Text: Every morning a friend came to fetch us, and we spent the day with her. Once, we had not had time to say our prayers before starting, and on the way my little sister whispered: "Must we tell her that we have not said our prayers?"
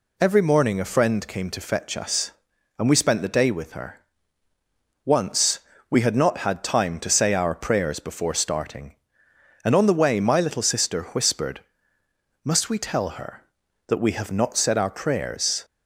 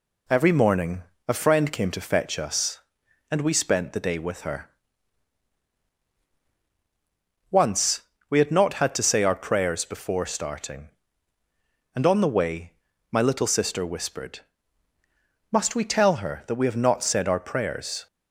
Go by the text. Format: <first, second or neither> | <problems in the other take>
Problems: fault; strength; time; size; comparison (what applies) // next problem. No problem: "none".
first | pauses between "morning" and "a"; slight; at 1.0 s; 0.24 s long // skips "time"; at 8.9 s // pauses between "way" and "my"; at 12.7 s; 0.40 s long